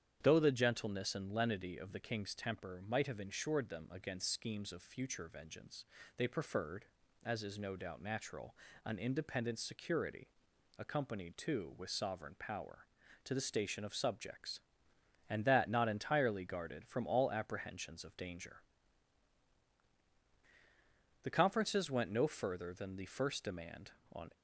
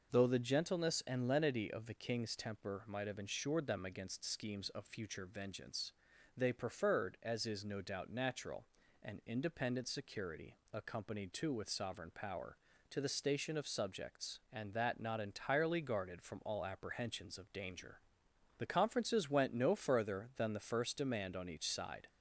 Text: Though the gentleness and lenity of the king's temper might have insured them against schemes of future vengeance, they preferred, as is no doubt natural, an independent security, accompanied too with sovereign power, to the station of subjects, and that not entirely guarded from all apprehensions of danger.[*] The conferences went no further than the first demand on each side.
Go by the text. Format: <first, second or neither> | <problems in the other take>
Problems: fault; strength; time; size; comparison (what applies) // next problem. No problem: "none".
second | starts louder than the rest; strong; until 1.2 s; 9 dB // stops before "each side"; at 24.3 s